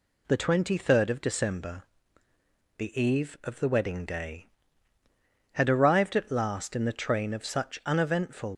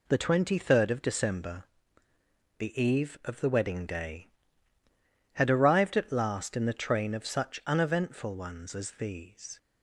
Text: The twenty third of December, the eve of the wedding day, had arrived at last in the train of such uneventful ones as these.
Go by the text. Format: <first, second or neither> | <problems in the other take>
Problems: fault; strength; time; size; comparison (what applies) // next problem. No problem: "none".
second | stops before "ones as these"; at 8.5 s